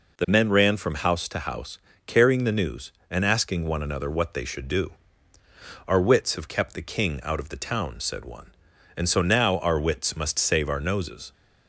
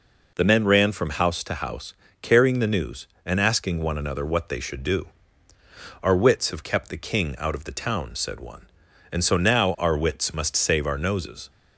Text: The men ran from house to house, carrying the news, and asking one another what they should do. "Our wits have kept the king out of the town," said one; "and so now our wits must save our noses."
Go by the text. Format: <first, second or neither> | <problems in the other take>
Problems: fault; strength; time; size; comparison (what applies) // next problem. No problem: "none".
neither | none